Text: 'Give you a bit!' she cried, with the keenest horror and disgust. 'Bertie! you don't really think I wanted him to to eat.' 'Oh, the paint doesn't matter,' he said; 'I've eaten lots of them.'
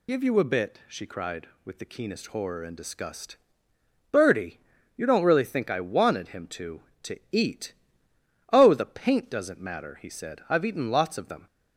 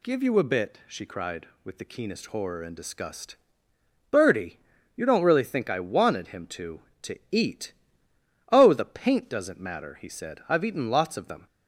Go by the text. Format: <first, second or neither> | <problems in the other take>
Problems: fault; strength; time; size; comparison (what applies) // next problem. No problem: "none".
second | loses the start of "Give"; at 0.0 s; 45 ms